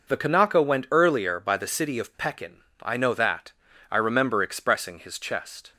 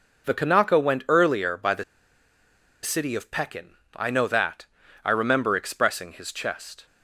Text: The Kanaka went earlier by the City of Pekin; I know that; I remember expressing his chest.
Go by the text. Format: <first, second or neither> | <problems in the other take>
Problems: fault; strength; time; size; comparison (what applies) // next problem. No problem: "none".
first | pauses between "the" and "City"; at 1.8 s; 0.99 s long